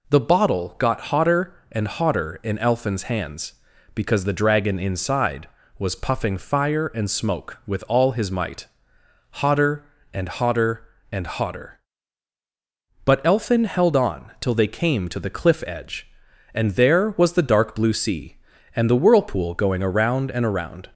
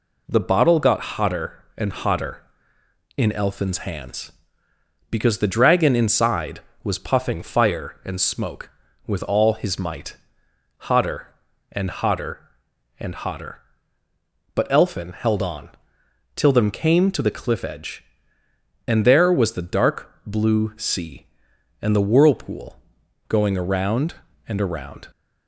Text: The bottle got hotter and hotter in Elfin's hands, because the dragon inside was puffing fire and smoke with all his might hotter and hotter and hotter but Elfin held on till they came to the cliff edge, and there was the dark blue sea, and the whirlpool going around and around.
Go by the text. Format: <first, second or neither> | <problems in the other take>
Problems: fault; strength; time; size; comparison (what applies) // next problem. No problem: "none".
first | pauses between "might" and "hotter"; noticeable; at 10.1 s; 0.74 s long; noticeable in the first // pauses between "on" and "till"; noticeable; at 15.6 s; 0.66 s long // says "them" for "they"; at 16.5 s // pauses between "dark" and "blue"; slight; at 20.1 s; 0.16 s long // pauses between "whirlpool" and "going"; noticeable; at 22.7 s; 0.50 s long